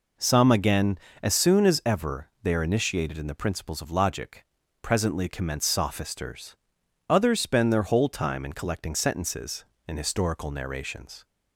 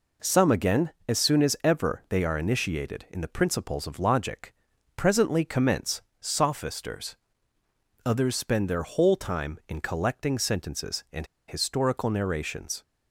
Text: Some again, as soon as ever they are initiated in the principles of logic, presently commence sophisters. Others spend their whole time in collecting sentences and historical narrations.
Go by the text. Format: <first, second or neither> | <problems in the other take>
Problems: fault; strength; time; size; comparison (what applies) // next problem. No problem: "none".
first | pauses between "commence" and "sophisters"; slight; at 6.0 s; 0.18 s long // pauses between "and" and "historical"; slight; at 11.2 s; 0.23 s long